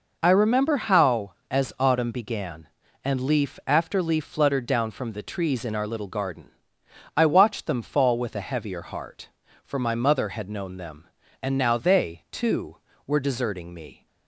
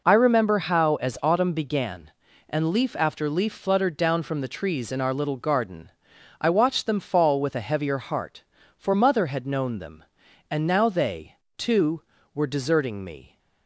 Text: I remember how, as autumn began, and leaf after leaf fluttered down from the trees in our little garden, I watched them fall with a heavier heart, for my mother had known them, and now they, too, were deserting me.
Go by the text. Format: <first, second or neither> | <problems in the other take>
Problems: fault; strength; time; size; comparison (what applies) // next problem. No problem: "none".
first | skips "my"; at 8.9 s